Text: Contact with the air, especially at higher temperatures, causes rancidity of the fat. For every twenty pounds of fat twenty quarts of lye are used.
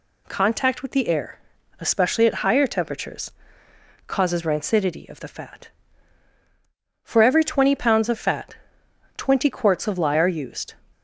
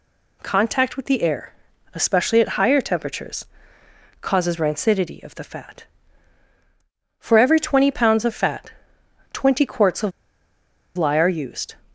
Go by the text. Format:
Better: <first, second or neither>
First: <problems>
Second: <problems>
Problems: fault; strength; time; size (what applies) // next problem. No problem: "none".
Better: first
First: pauses between "fat" and "twenty"; noticeable; at 8.5 s; 0.60 s long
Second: pauses between "fat" and "twenty"; noticeable; at 8.7 s; 0.60 s long // pauses between "of" and "lye"; noticeable; at 10.1 s; 0.86 s long